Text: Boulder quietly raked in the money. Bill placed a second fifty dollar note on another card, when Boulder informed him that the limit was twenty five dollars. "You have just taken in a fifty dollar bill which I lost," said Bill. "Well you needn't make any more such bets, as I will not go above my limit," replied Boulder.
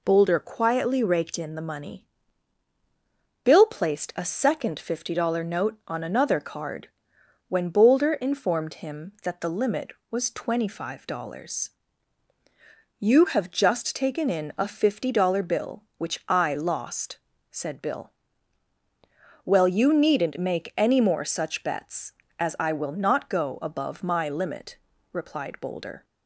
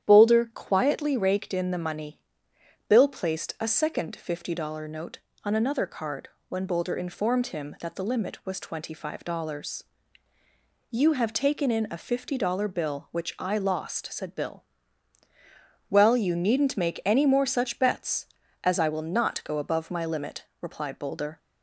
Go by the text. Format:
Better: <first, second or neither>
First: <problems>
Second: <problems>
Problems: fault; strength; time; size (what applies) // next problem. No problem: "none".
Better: first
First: none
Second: starts louder than the rest; strong; until 1.1 s; 10.5 dB // skips "just"; at 11.3 s